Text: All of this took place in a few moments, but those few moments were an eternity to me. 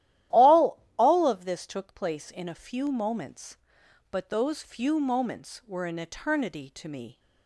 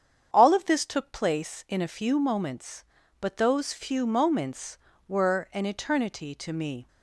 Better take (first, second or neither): second